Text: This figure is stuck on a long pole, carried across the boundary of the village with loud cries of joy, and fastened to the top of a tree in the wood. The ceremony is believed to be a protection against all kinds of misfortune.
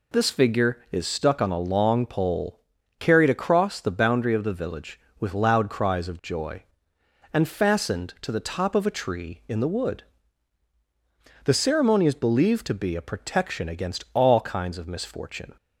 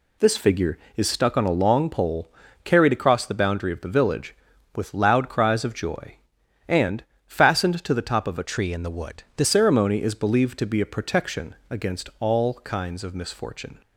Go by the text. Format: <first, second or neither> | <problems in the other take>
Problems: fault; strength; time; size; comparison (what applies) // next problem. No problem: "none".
first | pauses between "and" and "fastened"; slight; at 7.0 s; 0.22 s long // changes voice from "tree" to "The"; from 8.4 to 9.4 s; 1.0 s long